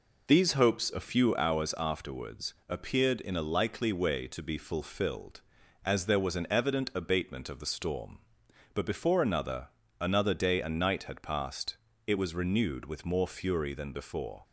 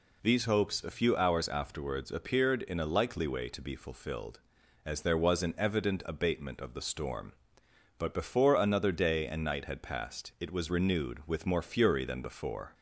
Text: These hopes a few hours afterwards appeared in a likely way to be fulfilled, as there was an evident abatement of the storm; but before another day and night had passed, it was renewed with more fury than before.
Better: second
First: pauses between "afterwards" and "appeared"; slight; at 2.5 s; 0.16 s long // says "another" twice; at 9.9 s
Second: none

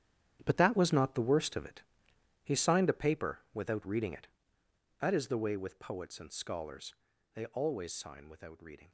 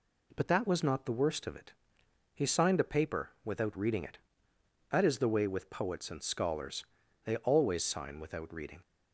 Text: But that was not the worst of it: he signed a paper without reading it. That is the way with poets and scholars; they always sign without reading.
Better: second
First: gets quieter; strong; throughout; 13 dB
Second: none

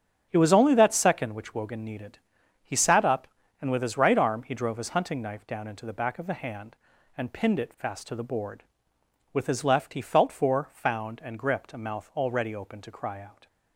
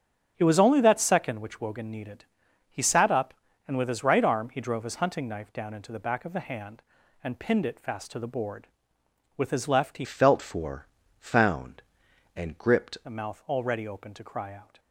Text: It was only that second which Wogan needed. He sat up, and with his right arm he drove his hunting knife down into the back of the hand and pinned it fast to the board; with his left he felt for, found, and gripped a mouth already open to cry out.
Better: first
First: starts louder than the rest; strong; until 1.3 s; 7.5 dB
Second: starts louder than the rest; strong; until 1.3 s; 8.5 dB // changes voice from "felt" to "gripped"; from 10.0 to 12.9 s; 2.9 s long

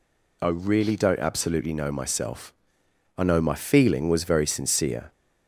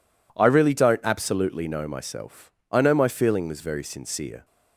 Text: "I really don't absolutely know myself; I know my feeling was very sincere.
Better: neither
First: none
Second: none

